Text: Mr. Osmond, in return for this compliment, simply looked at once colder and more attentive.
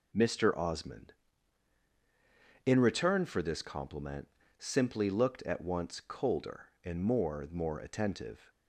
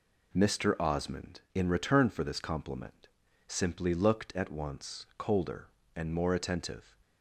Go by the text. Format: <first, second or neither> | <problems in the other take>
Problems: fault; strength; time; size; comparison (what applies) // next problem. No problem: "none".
second | says "more" twice; at 7.5 s